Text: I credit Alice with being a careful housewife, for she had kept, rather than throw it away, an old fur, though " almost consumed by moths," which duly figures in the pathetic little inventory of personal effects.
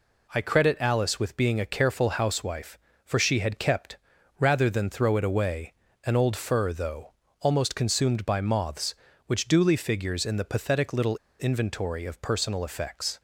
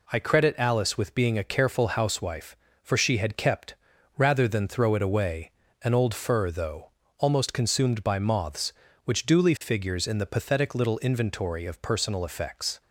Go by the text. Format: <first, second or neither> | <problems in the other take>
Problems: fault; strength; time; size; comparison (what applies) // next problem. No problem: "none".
second | pauses between "little" and "inventory"; slight; at 11.1 s; 0.23 s long